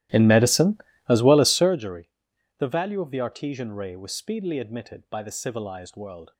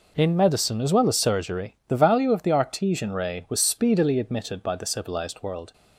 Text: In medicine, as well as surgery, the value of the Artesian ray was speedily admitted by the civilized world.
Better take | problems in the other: second | starts louder than the rest; strong; until 1.8 s; 15 dB

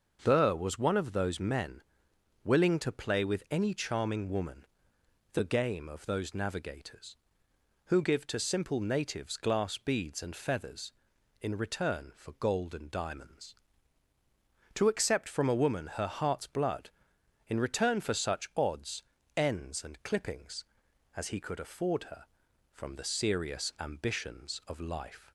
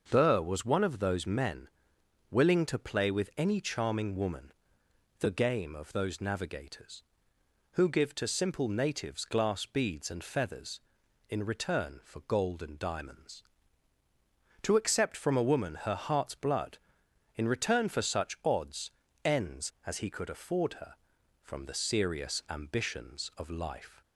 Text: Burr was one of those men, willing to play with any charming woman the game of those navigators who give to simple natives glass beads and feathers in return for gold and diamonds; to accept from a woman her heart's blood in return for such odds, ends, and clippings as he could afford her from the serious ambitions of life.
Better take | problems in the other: first | starts louder than the rest; until 1.0 s; 6.5 dB; also in the first // pauses between "woman" and "the"; noticeable; at 4.5 s; 0.66 s long; noticeable in the first // skips "and clippings"; at 19.7 s

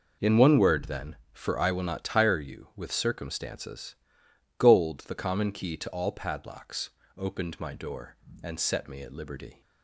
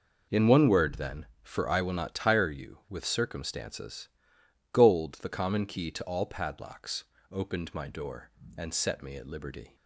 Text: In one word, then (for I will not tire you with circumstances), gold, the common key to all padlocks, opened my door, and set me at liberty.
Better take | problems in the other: neither | none

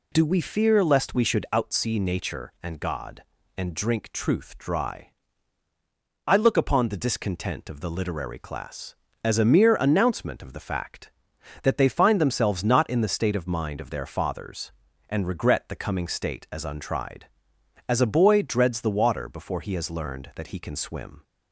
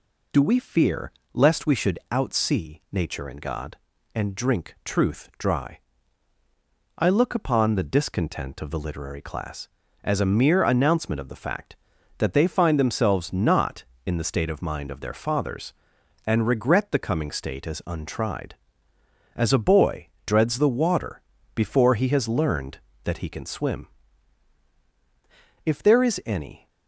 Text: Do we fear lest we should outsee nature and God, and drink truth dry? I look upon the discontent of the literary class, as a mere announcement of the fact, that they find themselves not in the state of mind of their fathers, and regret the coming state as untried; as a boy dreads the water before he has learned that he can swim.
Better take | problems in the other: first | pauses between "fear" and "lest"; slight; at 1.1 s; 0.24 s long // pauses between "boy" and "dreads"; slight; at 20.0 s; 0.20 s long // pauses between "water" and "before"; slight; at 21.2 s; 0.34 s long // goes on to say "If there is any"; noticeable; from 25.6 s on; 1.0 s long

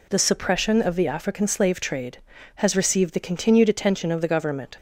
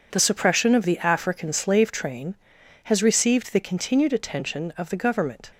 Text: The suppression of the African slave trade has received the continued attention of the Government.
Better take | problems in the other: first | says "train" for "trade"; at 1.9 s

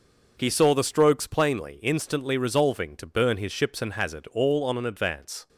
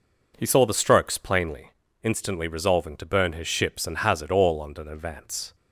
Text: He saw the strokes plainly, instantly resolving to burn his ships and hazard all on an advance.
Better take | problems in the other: neither | none

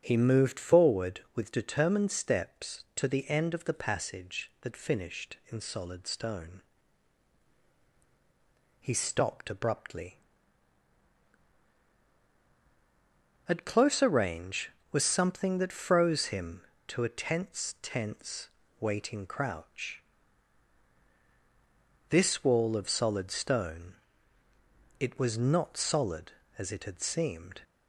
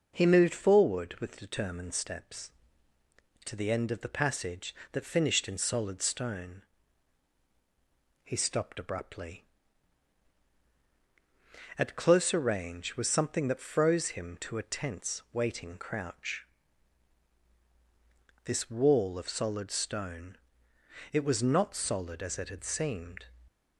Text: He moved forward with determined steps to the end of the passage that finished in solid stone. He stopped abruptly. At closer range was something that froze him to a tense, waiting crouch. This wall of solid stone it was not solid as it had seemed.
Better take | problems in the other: second | starts louder than the rest; until 1.0 s; 7 dB // says "tense" twice; at 17.8 s // pauses between "stone" and "it"; at 23.9 s; 1.0 s long; noticeable in the second

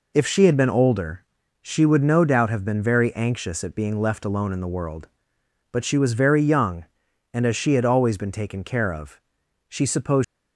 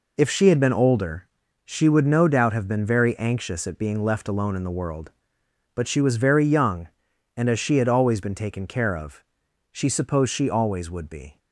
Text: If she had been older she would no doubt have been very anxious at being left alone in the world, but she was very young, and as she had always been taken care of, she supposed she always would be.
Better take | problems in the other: second | pauses between "older" and "she"; at 1.2 s; 0.38 s long; also in the second // stops before "she always would be"; at 10.2 s

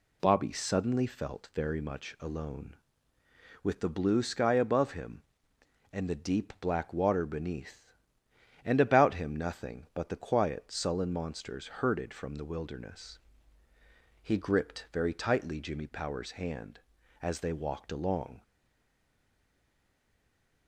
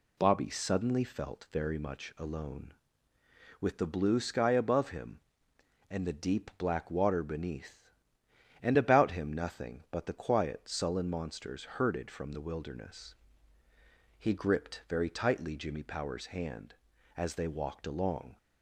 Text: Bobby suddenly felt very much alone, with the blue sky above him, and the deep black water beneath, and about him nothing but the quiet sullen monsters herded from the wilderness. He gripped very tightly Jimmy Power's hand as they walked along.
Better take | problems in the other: second | stays silent after the last word; from 18.4 s on; 2.2 s long

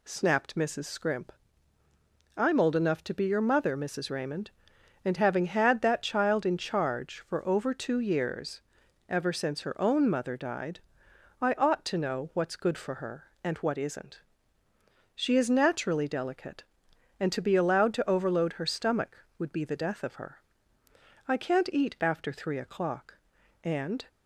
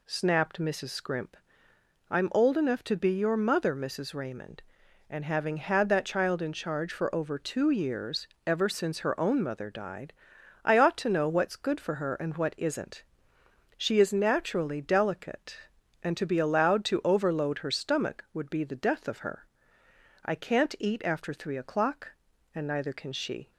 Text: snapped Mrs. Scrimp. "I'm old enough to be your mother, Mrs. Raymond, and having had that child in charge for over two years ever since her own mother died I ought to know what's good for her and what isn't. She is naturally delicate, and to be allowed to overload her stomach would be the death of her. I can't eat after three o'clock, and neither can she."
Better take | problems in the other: second | pauses between "years" and "ever"; noticeable; at 8.6 s; 0.46 s long; slight in the second // pauses between "died" and "I"; noticeable; at 10.7 s; 0.60 s long; noticeable in the second // stops before "neither can she"; at 24.0 s

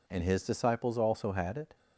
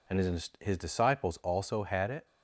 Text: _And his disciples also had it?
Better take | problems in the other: first | says "his" twice; at 0.5 s

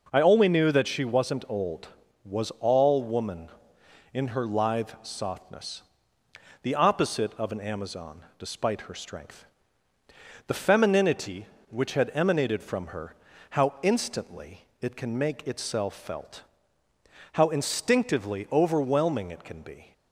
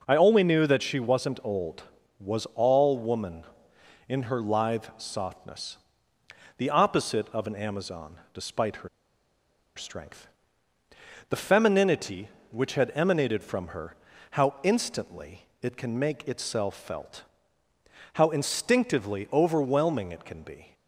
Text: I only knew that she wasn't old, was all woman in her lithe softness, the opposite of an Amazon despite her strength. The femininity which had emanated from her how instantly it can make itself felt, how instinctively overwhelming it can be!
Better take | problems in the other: first | pauses between "Amazon" and "despite"; slight; at 8.1 s; 0.18 s long; slight in the first // pauses between "her" and "strength"; noticeable; at 8.8 s; 0.87 s long // pauses between "her" and "how"; slight; at 13.9 s; 0.36 s long; slight in the first // pauses between "instantly" and "it"; slight; at 15.4 s; 0.16 s long; slight in the first

